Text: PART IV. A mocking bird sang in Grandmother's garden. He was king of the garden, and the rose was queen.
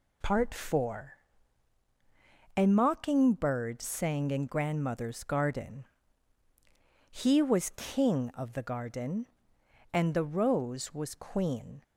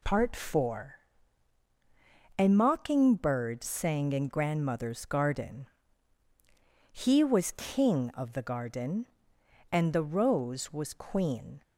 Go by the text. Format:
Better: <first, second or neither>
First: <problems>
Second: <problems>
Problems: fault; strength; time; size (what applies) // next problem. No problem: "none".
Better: neither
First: none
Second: none